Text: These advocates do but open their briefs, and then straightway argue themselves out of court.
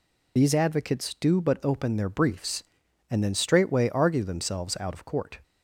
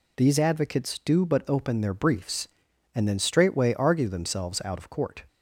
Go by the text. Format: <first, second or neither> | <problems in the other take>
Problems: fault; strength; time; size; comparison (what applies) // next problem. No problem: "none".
second | loses the start of "These"; at 0.3 s; 30 ms